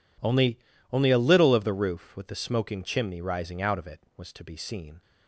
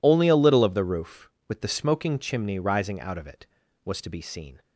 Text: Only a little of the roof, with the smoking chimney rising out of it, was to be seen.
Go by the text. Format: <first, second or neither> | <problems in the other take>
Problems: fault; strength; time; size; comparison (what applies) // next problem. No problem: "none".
second | says "Only" twice; at 0.9 s